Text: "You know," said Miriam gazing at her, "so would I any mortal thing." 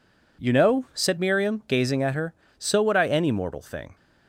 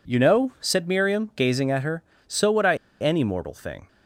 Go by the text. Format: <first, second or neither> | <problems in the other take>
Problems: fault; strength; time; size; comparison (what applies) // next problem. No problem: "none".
first | pauses between "I" and "any"; slight; at 2.7 s; 0.24 s long